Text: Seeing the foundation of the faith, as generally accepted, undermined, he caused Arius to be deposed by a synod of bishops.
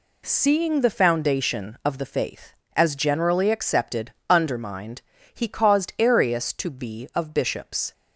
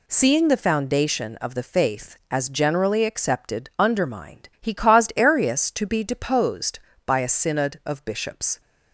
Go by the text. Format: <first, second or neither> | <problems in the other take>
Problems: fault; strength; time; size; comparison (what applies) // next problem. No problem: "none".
second | skips "deposed by a synod"; at 7.1 s